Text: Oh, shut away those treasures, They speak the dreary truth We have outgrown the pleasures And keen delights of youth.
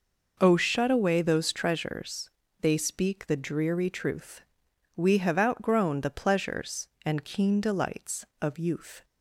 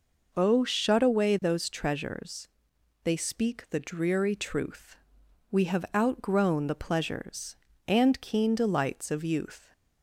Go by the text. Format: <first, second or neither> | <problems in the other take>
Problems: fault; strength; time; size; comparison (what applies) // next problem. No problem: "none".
neither | pauses between "truth" and "We"; noticeable; the same in both